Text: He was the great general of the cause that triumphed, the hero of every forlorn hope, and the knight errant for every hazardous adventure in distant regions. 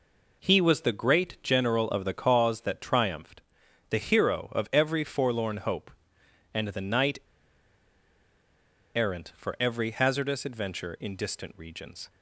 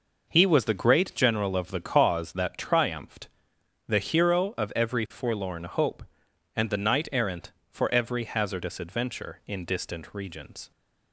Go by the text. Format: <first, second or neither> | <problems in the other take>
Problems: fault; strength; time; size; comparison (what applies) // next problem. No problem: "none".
second | pauses between "knight" and "errant"; strong; at 7.1 s; 1.7 s long